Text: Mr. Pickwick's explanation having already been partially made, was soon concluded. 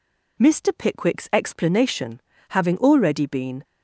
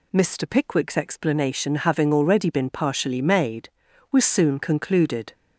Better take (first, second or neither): second